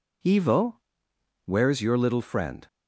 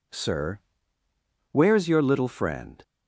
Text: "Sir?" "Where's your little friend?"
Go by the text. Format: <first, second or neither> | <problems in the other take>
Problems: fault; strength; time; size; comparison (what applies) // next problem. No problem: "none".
second | says "Evo" for "Sir"; at 0.2 s